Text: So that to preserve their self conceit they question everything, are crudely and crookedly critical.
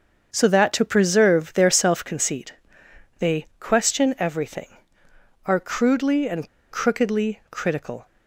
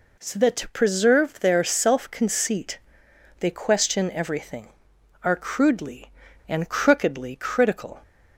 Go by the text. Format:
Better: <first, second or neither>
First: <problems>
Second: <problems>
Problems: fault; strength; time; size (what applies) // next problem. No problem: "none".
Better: second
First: starts louder than the rest; until 1.3 s; 6.5 dB // pauses between "conceit" and "they"; noticeable; at 2.5 s; 0.64 s long // pauses between "and" and "crookedly"; slight; at 6.4 s; 0.23 s long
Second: pauses between "conceit" and "they"; noticeable; at 2.7 s; 0.58 s long